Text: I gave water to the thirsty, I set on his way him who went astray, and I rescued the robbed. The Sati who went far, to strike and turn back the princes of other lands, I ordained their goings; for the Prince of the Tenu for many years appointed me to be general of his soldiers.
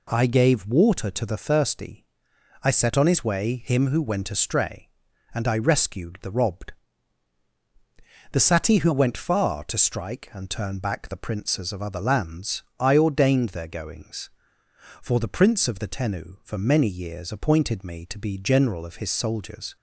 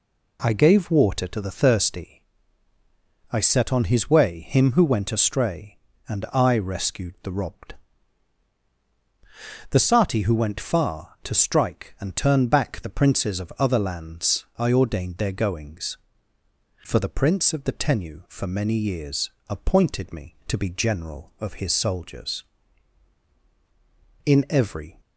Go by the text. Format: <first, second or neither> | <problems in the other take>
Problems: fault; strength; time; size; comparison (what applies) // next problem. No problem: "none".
first | pauses between "years" and "appointed"; slight; at 19.2 s; 0.18 s long // goes on to say "In every"; noticeable; from 24.2 s on; 0.72 s long